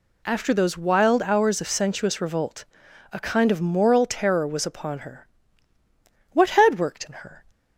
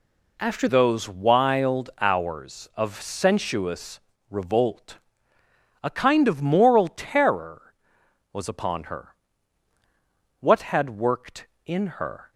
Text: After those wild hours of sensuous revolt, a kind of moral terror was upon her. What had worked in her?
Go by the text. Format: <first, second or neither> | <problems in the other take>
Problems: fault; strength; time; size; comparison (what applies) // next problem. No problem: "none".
first | changes voice at "those"; from 0.6 s on; 11.7 s long // pauses between "sensuous" and "revolt"; slight; at 4.0 s; 0.28 s long